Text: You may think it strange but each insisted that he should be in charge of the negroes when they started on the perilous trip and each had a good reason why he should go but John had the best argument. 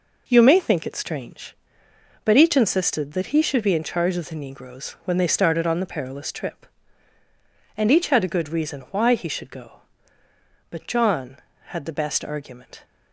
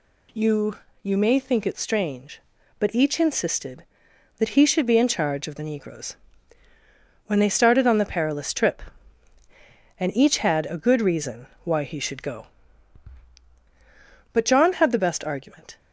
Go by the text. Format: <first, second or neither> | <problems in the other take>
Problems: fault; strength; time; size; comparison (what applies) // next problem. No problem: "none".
first | says "You" twice; at 1.0 s // pauses between "negroes" and "when"; at 6.1 s; 1.1 s long // pauses between "reason" and "why"; slight; at 11.4 s; 0.16 s long